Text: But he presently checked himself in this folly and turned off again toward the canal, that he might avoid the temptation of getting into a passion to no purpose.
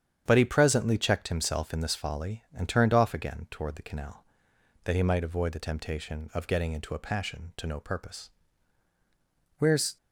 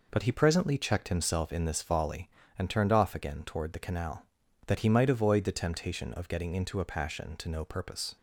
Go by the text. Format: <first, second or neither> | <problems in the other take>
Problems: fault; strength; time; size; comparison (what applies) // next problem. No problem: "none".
second | starts louder than the rest; strong; until 1.2 s; 9 dB // goes on to say "Where's"; slight; from 9.5 s on; 0.38 s long